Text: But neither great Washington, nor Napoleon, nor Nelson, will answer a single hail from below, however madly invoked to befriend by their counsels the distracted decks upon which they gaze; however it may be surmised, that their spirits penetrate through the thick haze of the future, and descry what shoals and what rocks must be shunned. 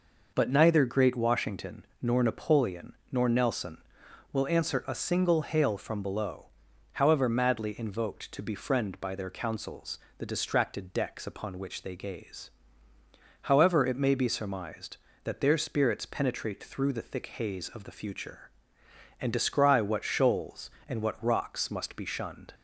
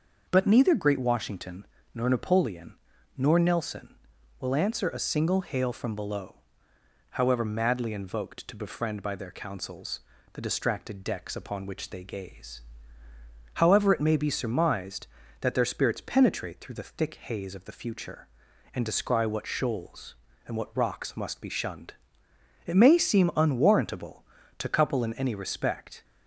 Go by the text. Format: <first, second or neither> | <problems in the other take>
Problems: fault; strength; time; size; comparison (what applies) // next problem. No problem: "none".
first | starts louder than the rest; noticeable; until 1.3 s; 6 dB // pauses between "counsels" and "the"; slight; at 9.9 s; 0.34 s long; slight in the first // goes on to say "It may seem unwarrantable to couple in any respect"; strong; from 22.6 s on; 3.3 s long